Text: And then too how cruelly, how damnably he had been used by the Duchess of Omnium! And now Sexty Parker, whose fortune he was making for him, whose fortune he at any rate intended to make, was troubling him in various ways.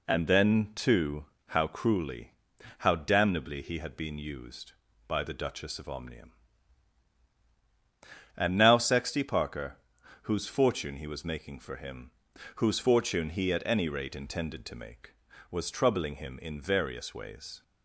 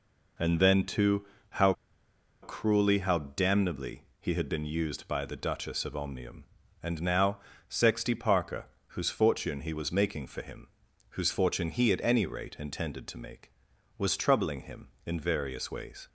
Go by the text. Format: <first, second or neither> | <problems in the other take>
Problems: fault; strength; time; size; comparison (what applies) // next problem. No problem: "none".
first | pauses between "too" and "how"; slight; at 1.2 s; 0.26 s long; slight in the first // pauses between "how" and "cruelly"; noticeable; at 1.7 s; 0.69 s long // pauses between "damnably" and "he"; slight; at 4.0 s; 0.16 s long // pauses between "now" and "Sexty"; slight; at 7.3 s; 0.30 s long